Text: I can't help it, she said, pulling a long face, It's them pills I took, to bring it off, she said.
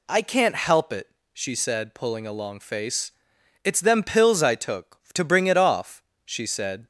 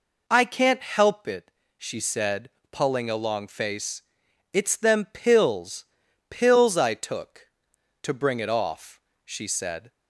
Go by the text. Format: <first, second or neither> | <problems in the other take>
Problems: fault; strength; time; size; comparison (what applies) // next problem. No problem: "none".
first | says "pills" twice; at 6.2 s